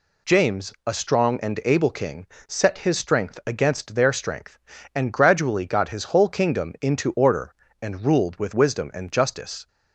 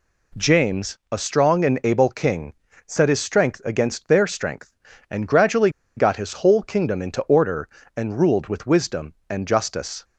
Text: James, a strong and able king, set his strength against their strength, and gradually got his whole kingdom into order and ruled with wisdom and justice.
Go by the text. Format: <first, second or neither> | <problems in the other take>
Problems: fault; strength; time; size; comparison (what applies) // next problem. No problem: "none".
first | pauses between "gradually" and "got"; slight; at 5.6 s; 0.27 s long